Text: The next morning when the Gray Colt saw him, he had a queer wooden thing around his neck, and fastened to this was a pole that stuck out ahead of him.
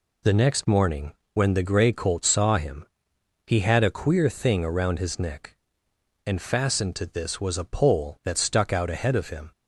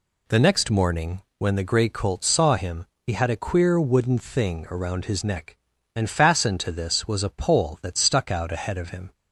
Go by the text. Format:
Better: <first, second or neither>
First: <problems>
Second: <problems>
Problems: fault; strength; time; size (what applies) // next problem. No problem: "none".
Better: second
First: pauses between "morning" and "when"; slight; at 1.1 s; 0.22 s long // skips "wooden"; at 4.2 s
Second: pauses between "morning" and "when"; slight; at 1.1 s; 0.18 s long